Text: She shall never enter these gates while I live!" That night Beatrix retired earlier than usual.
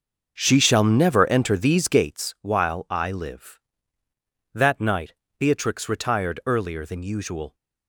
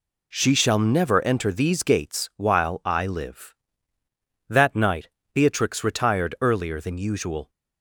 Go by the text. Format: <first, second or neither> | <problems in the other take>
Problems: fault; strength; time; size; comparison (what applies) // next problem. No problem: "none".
second | starts louder than the rest; noticeable; until 2.2 s; 6 dB // pauses between "night" and "Beatrix"; slight; at 5.1 s; 0.24 s long; slight in the second